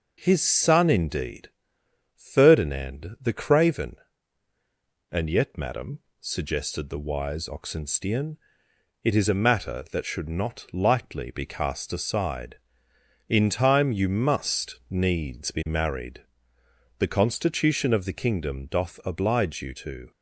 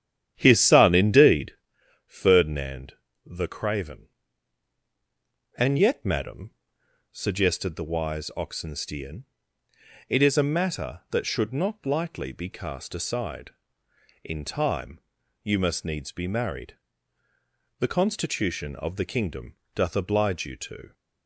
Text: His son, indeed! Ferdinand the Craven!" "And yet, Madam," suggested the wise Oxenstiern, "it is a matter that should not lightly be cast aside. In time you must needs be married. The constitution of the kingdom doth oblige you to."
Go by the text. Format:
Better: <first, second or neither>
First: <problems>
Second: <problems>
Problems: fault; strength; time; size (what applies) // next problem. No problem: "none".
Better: first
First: none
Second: starts louder than the rest; strong; until 1.7 s; 10 dB // pauses between "Ferdinand" and "the"; slight; at 2.9 s; 0.32 s long // pauses between "time" and "you"; at 14.9 s; 0.44 s long // pauses between "kingdom" and "doth"; slight; at 19.5 s; 0.20 s long